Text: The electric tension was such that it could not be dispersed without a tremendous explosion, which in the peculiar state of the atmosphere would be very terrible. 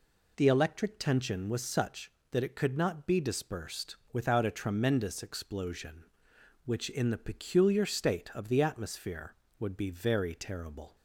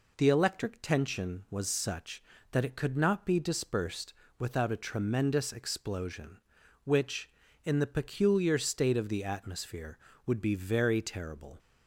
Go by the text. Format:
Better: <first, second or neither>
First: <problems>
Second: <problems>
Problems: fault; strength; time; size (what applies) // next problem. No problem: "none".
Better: neither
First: pauses between "dispersed" and "without"; slight; at 3.9 s; 0.16 s long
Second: pauses between "dispersed" and "without"; slight; at 4.1 s; 0.26 s long